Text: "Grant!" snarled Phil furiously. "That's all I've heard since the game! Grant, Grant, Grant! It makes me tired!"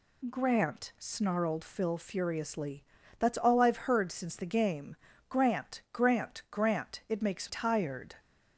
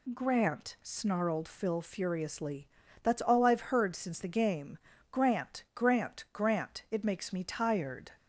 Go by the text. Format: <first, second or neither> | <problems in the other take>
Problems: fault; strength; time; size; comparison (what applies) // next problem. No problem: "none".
second | skips "me"; at 7.4 s